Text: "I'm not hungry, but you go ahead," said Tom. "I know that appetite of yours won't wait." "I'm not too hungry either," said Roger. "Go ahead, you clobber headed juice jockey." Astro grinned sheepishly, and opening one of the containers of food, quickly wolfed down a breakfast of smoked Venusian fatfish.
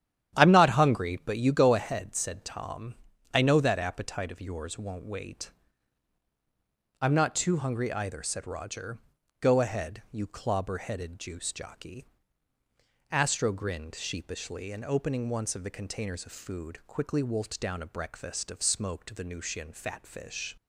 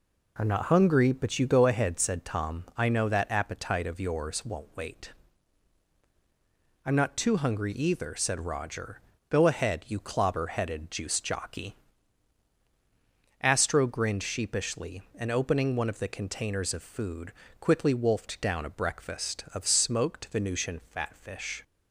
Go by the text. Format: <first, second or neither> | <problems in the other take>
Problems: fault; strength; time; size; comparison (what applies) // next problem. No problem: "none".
second | starts louder than the rest; strong; until 1.4 s; 10.5 dB // says "once" for "one"; at 15.2 s